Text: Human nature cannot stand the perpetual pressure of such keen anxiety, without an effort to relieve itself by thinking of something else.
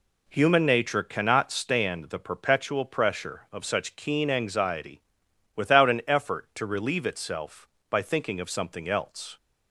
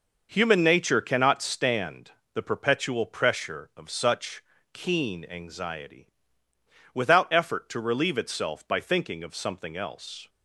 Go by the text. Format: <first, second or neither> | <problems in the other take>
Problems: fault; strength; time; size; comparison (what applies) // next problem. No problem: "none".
first | pauses between "stand" and "the"; slight; at 2.1 s; 0.24 s long // pauses between "such" and "keen"; slight; at 4.4 s; 0.30 s long // skips "an"; at 7.3 s